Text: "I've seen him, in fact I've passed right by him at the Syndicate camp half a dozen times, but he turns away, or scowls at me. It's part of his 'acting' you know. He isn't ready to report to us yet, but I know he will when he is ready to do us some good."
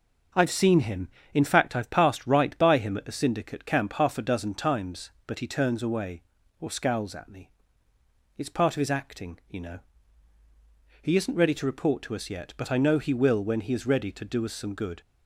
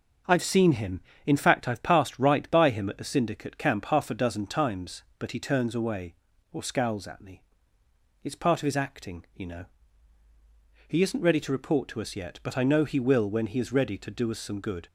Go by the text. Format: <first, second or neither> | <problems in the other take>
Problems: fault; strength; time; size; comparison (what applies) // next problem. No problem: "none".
neither | starts louder than the rest; the same in both